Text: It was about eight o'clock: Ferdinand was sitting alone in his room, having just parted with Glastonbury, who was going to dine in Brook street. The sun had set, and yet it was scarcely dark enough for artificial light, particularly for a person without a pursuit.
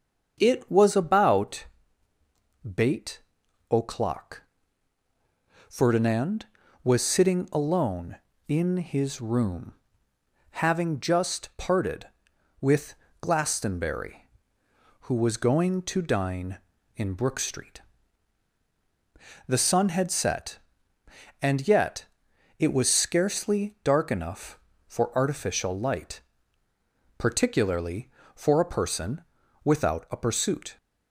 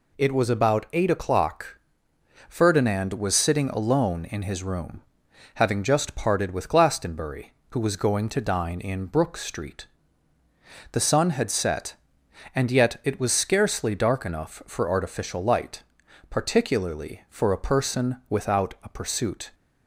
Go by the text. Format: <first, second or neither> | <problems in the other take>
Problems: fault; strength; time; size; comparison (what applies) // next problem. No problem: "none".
second | starts louder than the rest; until 1.4 s; 7 dB // says "bait" for "eight"; at 2.6 s // pauses between "with" and "Glastonbury"; slight; at 12.9 s; 0.24 s long // pauses between "yet" and "it"; noticeable; at 22.0 s; 0.54 s long // pauses between "person" and "without"; at 29.2 s; 0.42 s long